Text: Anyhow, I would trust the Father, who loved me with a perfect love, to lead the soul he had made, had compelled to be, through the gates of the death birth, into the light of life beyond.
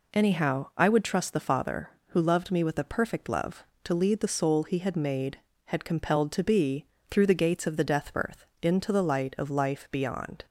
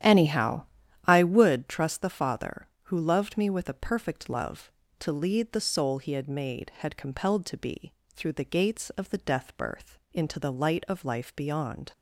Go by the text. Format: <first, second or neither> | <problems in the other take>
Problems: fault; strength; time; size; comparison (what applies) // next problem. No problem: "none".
first | starts louder than the rest; strong; until 1.5 s; 11 dB